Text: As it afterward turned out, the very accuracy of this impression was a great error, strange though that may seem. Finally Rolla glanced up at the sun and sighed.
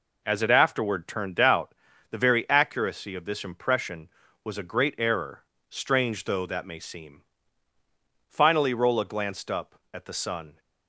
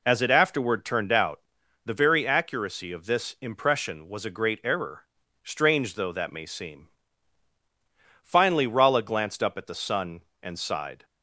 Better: second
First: stops before "and sighed"; at 10.5 s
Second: none

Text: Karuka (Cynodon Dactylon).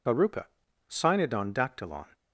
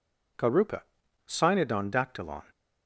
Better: second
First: loses the start of "Karuka"; at 0.0 s; 60 ms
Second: none

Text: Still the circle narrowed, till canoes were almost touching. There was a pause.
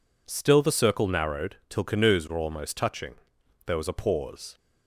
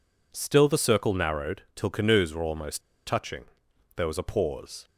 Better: first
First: none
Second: pauses between "almost" and "touching"; slight; at 2.7 s; 0.26 s long

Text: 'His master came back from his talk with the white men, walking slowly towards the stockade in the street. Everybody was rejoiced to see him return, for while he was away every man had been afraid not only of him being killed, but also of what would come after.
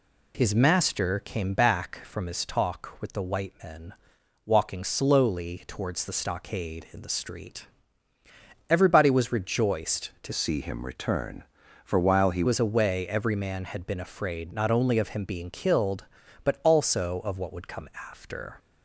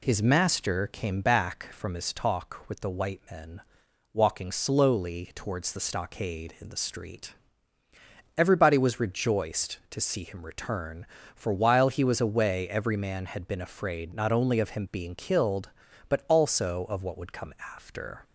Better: second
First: changes voice from "see" to "he"; from 10.3 to 12.4 s; 2.1 s long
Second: none

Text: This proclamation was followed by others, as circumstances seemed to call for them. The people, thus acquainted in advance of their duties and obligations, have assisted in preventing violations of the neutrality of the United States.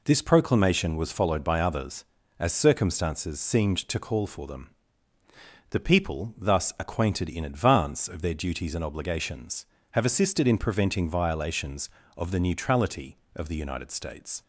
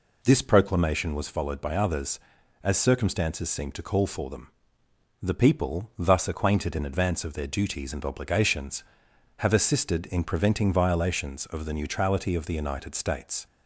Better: neither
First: none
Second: none

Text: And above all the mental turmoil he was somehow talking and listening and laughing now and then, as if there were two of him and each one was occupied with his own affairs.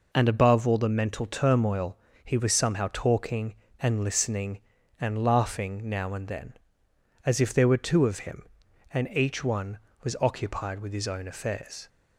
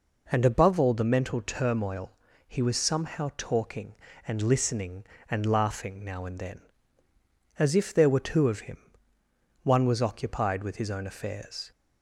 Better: first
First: pauses between "turmoil" and "he"; slight; at 1.9 s; 0.28 s long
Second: pauses between "turmoil" and "he"; slight; at 2.1 s; 0.32 s long // skips "and each"; at 9.1 s

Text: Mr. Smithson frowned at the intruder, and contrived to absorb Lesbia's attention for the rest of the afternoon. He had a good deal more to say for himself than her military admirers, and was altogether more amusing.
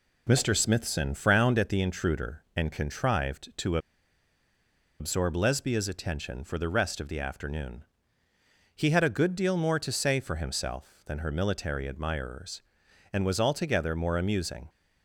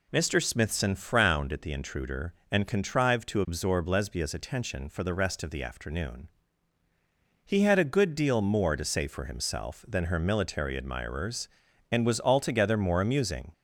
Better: second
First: pauses between "to" and "absorb"; at 3.7 s; 1.2 s long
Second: none

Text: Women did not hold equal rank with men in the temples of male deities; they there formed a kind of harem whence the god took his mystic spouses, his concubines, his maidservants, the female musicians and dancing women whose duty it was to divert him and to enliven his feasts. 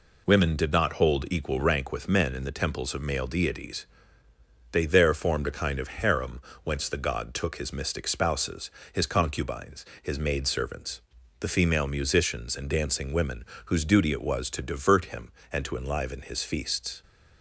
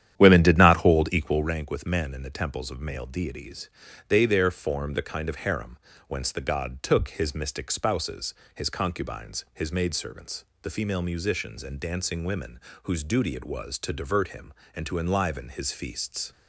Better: first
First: pauses between "harem" and "whence"; slight; at 6.3 s; 0.24 s long // pauses between "women" and "whose"; slight; at 13.4 s; 0.22 s long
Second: starts louder than the rest; strong; until 1.6 s; 10.5 dB // pauses between "harem" and "whence"; slight; at 5.7 s; 0.30 s long // pauses between "women" and "whose"; slight; at 12.6 s; 0.22 s long

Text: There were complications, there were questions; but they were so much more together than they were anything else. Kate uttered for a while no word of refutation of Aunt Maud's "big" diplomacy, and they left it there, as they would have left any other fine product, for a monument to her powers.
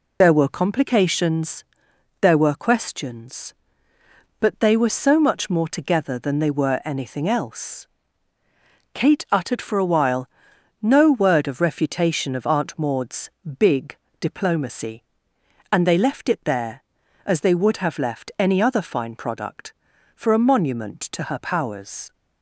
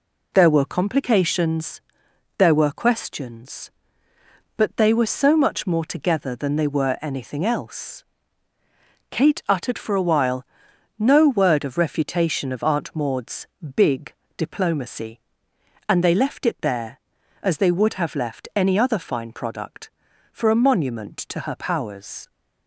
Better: second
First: loses the start of "There"; at 0.2 s; 25 ms // pauses between "while" and "no"; noticeable; at 10.2 s; 0.52 s long // pauses between "Maud's" and "big"; slight; at 13.2 s; 0.30 s long // pauses between "big" and "diplomacy"; slight; at 13.9 s; 0.24 s long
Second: pauses between "while" and "no"; noticeable; at 10.4 s; 0.52 s long // pauses between "Maud's" and "big"; slight; at 13.4 s; 0.30 s long // pauses between "big" and "diplomacy"; slight; at 14.1 s; 0.24 s long

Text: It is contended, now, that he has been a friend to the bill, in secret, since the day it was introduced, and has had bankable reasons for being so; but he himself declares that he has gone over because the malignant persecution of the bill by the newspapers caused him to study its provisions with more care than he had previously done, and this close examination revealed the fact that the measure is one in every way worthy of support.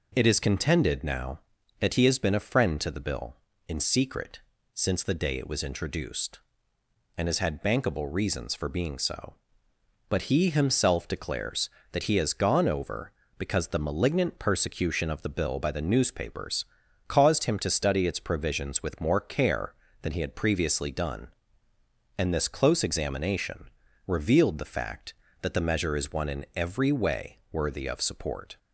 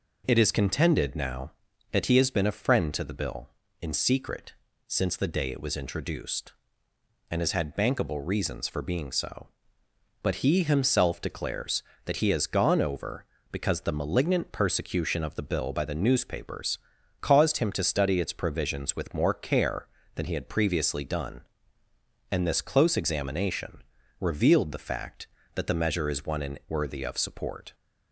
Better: first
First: pauses between "newspapers" and "caused"; at 16.6 s; 0.42 s long // pauses between "examination" and "revealed"; slight; at 23.6 s; 0.36 s long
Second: pauses between "newspapers" and "caused"; at 16.7 s; 0.42 s long // pauses between "examination" and "revealed"; slight; at 23.8 s; 0.36 s long // skips "every way"; at 26.6 s

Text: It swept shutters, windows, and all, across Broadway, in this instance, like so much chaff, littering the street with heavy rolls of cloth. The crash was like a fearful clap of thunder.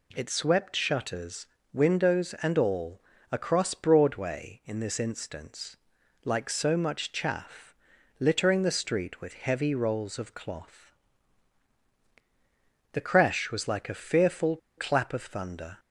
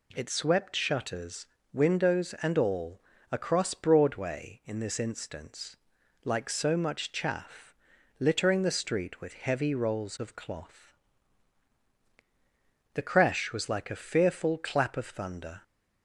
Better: second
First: pauses between "fearful" and "clap"; slight; at 14.5 s; 0.20 s long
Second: none

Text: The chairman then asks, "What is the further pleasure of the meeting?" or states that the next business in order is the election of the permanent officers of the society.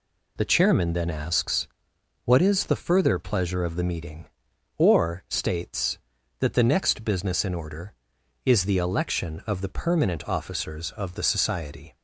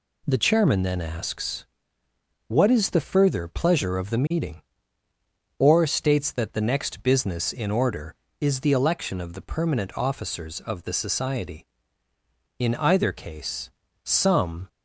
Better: first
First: none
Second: goes on to say "In either case some"; strong; from 12.5 s on; 2.0 s long

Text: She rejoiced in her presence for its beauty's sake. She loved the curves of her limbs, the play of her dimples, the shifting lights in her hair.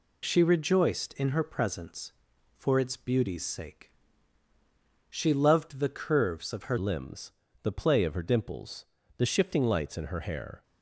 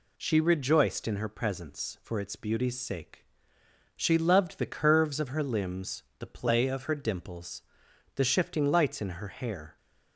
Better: second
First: changes voice at "limbs"; from 6.7 s on; 3.9 s long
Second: none

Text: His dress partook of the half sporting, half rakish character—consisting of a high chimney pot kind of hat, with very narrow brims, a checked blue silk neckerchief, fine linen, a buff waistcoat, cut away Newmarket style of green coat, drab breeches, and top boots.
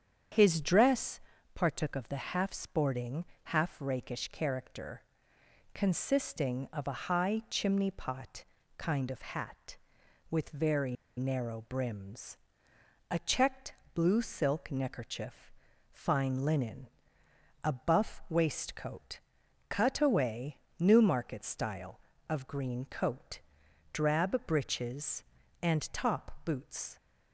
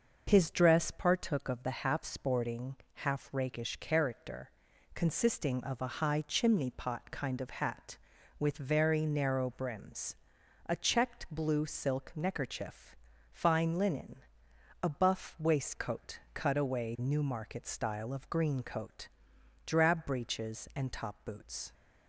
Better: second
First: starts louder than the rest; strong; until 1.6 s; 8 dB // pauses between "dress" and "partook"; slight; at 1.2 s; 0.32 s long // pauses between "pot" and "kind"; slight; at 8.4 s; 0.34 s long // pauses between "very" and "narrow"; slight; at 10.9 s; 0.23 s long // pauses between "checked" and "blue"; slight; at 13.7 s; 0.22 s long // pauses between "away" and "Newmarket"; slight; at 20.5 s; 0.22 s long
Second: starts louder than the rest; noticeable; until 1.2 s; 6 dB

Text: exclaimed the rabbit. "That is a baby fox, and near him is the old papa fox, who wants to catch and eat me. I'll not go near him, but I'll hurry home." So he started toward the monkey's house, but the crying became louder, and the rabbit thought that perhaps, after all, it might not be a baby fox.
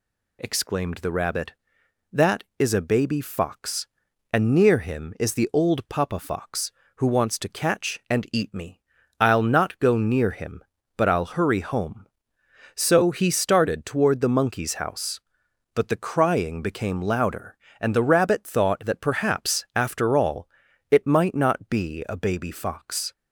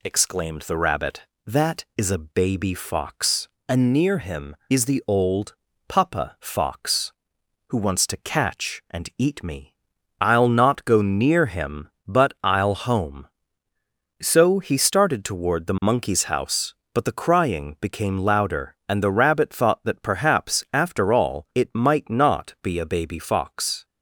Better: first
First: none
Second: pauses between "old" and "papa"; slight; at 5.5 s; 0.34 s long // skips "hurry"; at 12.7 s

